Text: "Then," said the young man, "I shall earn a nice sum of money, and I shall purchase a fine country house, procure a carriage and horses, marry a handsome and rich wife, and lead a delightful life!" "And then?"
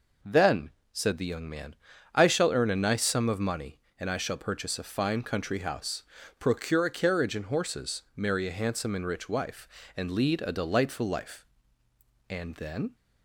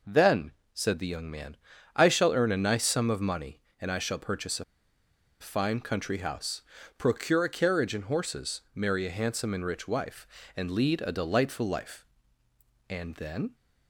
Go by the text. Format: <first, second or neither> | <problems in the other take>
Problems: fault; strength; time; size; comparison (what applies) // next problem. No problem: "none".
first | pauses between "a" and "fine"; noticeable; at 4.6 s; 0.76 s long